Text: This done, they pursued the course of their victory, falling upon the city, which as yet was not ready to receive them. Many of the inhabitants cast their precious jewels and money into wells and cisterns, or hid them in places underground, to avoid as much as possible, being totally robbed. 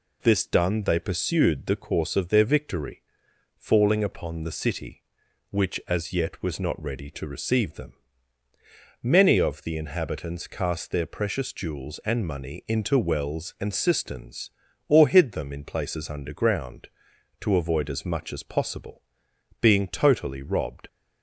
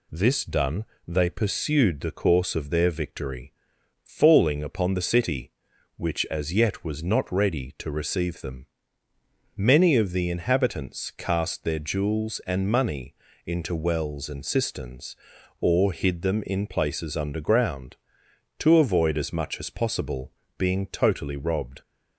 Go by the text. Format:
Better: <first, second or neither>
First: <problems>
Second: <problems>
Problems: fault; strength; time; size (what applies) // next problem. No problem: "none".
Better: first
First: none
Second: skips "precious"; at 11.7 s // pauses between "money" and "into"; slight; at 13.1 s; 0.32 s long